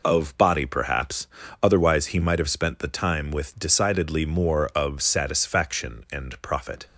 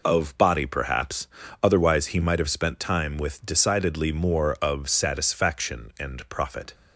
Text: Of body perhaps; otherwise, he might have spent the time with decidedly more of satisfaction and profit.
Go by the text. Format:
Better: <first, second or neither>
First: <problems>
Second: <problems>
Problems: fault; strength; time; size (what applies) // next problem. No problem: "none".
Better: first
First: none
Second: skips "the"; at 2.7 s